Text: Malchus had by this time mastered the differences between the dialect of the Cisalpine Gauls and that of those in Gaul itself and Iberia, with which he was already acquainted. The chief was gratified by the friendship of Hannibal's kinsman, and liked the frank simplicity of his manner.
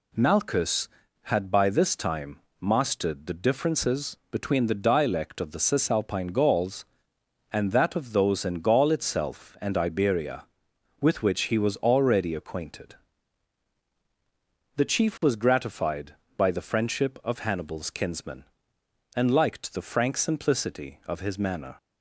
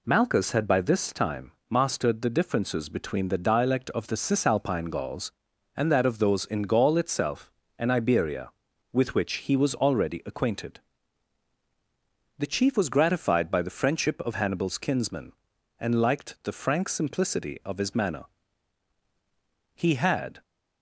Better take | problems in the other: first | pauses between "time" and "mastered"; slight; at 1.5 s; 0.18 s long; slight in the first // goes on to say "He had"; noticeable; from 19.7 s on; 0.66 s long

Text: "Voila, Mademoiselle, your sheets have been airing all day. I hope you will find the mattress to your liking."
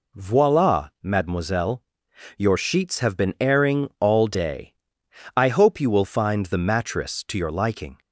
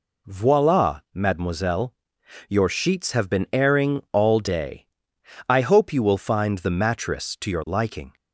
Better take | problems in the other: neither | none

